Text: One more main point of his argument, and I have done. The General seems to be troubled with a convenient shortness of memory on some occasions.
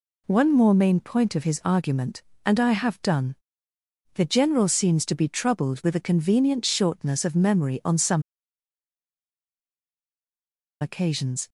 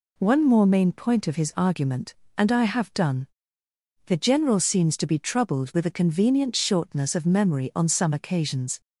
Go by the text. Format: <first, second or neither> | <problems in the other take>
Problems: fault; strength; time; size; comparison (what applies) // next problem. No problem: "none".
second | pauses between "some" and "occasions"; strong; at 8.2 s; 2.5 s long